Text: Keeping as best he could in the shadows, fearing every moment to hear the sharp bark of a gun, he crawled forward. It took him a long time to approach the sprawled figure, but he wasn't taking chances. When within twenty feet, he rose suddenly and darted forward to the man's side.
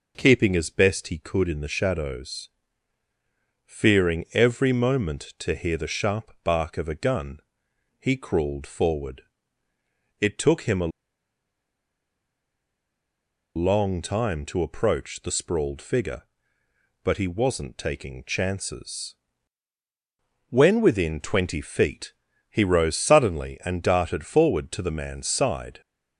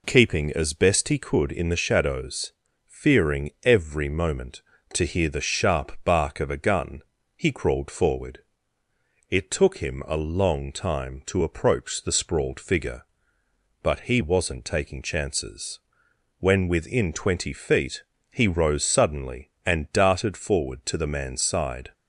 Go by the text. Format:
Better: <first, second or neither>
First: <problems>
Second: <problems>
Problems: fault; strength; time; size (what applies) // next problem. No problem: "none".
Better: second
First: pauses between "a" and "long"; strong; at 10.9 s; 2.6 s long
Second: none